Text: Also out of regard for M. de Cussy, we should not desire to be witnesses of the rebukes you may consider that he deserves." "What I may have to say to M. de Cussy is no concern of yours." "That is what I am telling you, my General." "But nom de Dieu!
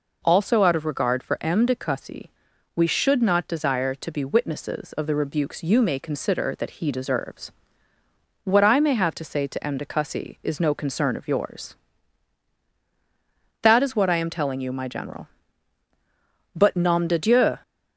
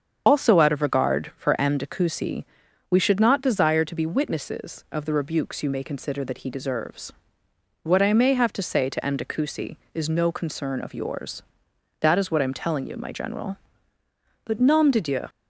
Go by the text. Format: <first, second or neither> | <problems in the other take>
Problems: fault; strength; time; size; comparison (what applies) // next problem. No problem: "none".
first | loses the start of "Also"; at 0.2 s; 65 ms // starts louder than the rest; until 1.2 s; 7 dB